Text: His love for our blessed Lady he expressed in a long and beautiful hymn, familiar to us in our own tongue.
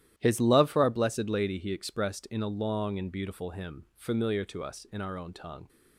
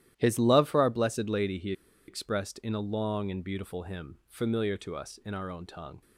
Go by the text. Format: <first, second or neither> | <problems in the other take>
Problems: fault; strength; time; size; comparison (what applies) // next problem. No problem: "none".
first | starts louder than the rest; strong; until 1.1 s; 12.5 dB; strong in the first // pauses between "he" and "expressed"; slight; at 1.7 s; 0.35 s long